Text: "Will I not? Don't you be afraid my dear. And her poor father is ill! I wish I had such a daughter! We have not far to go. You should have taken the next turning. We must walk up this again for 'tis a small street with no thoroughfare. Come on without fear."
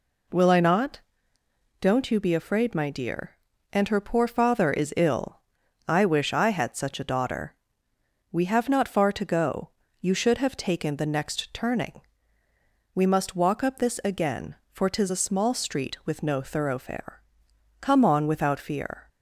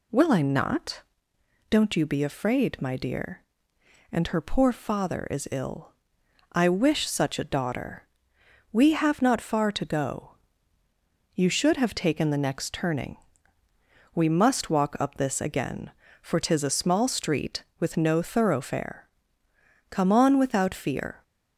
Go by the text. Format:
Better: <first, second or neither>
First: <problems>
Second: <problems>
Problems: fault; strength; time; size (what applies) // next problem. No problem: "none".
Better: first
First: none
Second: skips "I had"; at 7.0 s